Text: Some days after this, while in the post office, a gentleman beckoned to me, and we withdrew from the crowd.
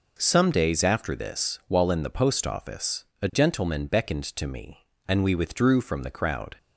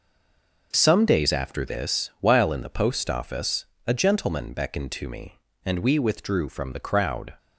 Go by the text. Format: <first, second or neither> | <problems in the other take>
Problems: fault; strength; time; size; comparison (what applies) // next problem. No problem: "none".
first | stays silent before the first word; slight; until 0.7 s; 0.7 s long